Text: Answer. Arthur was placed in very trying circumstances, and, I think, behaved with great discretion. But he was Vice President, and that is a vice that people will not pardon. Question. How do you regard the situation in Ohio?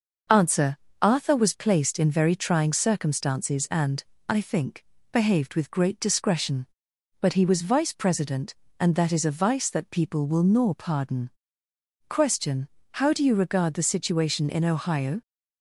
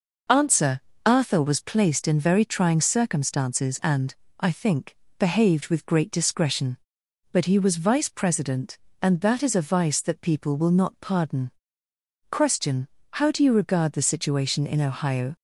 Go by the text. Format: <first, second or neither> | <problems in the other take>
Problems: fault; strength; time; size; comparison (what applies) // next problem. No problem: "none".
second | says "nor" for "not"; at 10.4 s